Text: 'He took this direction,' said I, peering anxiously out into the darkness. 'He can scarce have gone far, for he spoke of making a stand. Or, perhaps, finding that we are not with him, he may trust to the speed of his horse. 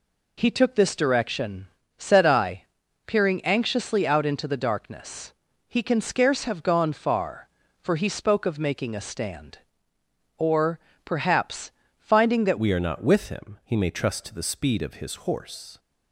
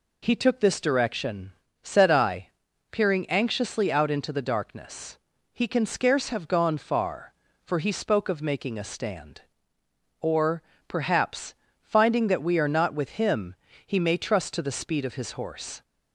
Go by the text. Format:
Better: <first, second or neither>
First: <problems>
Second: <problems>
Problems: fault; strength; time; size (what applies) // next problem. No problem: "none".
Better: second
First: changes voice at "we"; from 12.5 s on; 3.2 s long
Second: none